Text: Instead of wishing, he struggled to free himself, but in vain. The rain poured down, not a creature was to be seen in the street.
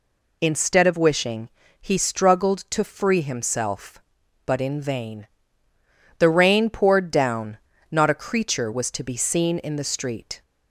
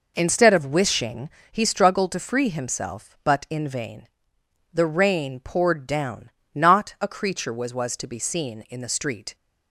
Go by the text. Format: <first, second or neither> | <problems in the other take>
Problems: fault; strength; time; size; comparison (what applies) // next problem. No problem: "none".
first | says "was" twice; at 7.7 s